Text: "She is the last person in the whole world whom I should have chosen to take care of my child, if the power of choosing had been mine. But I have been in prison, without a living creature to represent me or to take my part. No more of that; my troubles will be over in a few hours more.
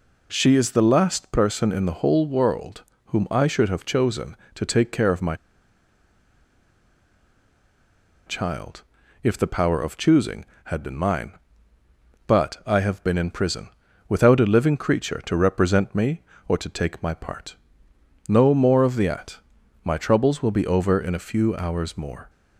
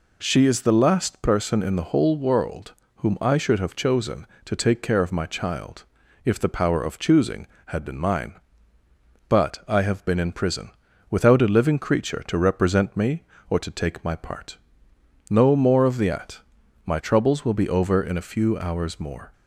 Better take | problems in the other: second | pauses between "world" and "whom"; slight; at 2.8 s; 0.24 s long; slight in the second // pauses between "my" and "child"; strong; at 5.3 s; 2.9 s long

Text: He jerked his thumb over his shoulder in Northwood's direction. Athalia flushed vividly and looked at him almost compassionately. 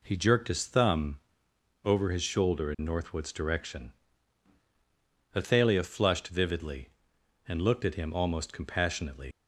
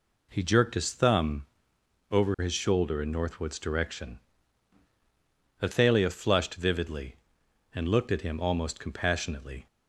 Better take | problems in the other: second | pauses between "thumb" and "over"; noticeable; at 1.2 s; 0.64 s long; noticeable in the second // leaves "compassionately" unfinished; at 9.3 s; 90 ms

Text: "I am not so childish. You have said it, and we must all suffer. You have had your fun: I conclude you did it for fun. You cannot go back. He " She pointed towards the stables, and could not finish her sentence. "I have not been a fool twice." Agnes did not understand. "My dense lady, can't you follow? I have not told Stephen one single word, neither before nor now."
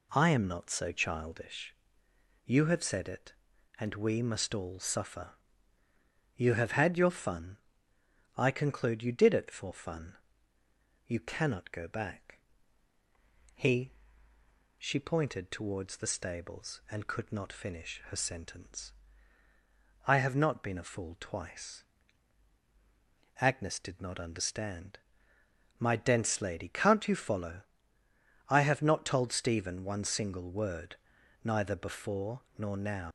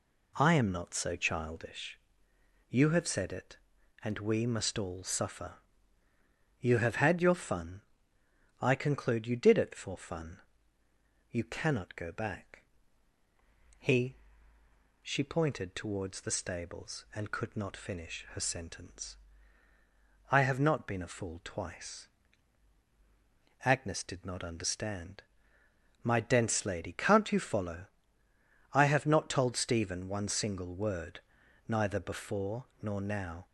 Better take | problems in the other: second | pauses between "before" and "nor"; slight; at 32.4 s; 0.16 s long; slight in the second // leaves "now" unfinished; at 33.0 s; 100 ms

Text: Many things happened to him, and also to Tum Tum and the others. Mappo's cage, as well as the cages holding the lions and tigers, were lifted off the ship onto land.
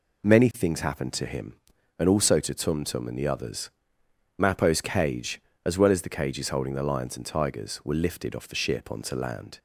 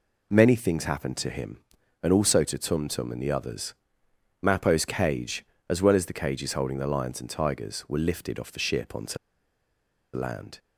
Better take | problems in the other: first | pauses between "onto" and "land"; at 9.1 s; 0.98 s long

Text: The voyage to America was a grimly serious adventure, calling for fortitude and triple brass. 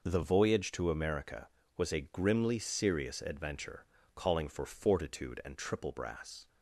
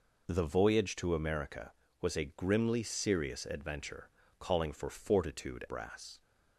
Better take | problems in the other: first | skips "and triple"; at 5.6 s

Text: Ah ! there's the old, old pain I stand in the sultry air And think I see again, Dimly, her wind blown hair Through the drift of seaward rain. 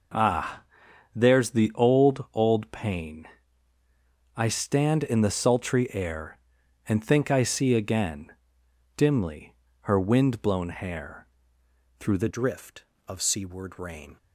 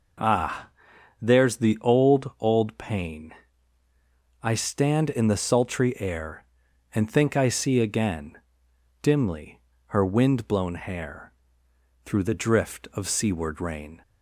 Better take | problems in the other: second | pauses between "pain" and "I"; at 3.2 s; 1.0 s long; also in the second // pauses between "hair" and "Through"; noticeable; at 11.2 s; 0.72 s long; noticeable in the second // changes voice at "drift"; from 12.3 s on; 1.8 s long

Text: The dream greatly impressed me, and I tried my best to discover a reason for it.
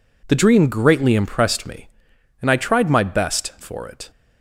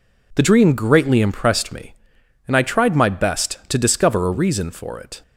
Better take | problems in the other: second | skips "to discover a reason"; at 3.5 s

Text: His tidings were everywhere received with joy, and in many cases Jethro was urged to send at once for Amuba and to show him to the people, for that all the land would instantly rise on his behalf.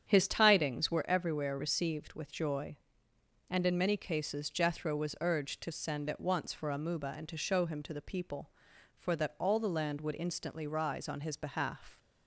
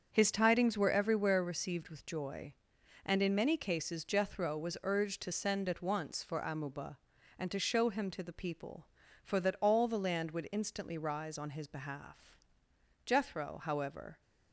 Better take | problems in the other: first | starts louder than the rest; until 1.1 s; 7 dB; strong in the first // goes on to say "Jethro however"; noticeable; from 13.0 s on; 1.1 s long

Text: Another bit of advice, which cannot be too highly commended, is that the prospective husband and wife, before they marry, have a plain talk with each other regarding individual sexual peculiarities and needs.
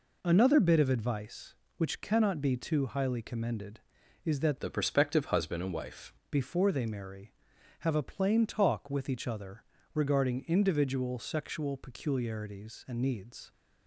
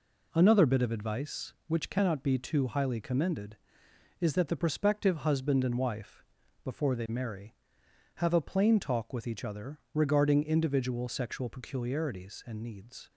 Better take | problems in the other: second | changes voice from "the" to "wife"; from 4.5 to 6.1 s; 1.6 s long // pauses between "other" and "regarding"; slight; at 9.6 s; 0.32 s long

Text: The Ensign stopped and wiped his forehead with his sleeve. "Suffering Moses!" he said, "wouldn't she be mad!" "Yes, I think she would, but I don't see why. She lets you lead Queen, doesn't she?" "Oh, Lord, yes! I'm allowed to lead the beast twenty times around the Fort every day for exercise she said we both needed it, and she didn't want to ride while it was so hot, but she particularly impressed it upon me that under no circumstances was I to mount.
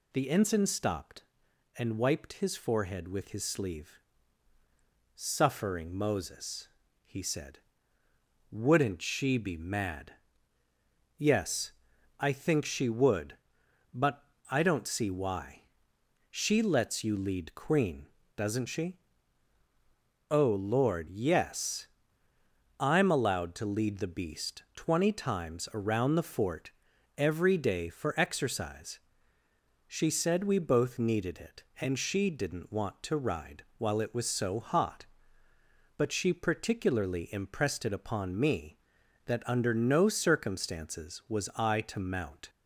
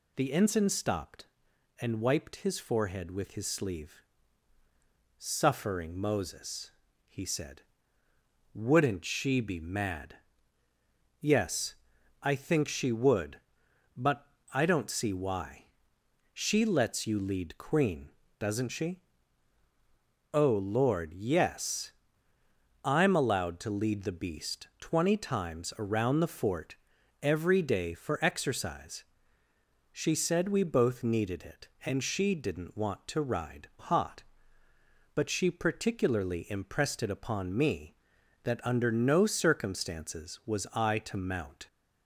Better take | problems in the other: first | pauses between "but" and "I"; slight; at 14.2 s; 0.24 s long; slight in the first // pauses between "Fort" and "every"; noticeable; at 26.7 s; 0.46 s long; noticeable in the first // pauses between "exercise" and "she"; noticeable; at 29.0 s; 0.90 s long; noticeable in the first // skips "while it was so"; at 33.7 s

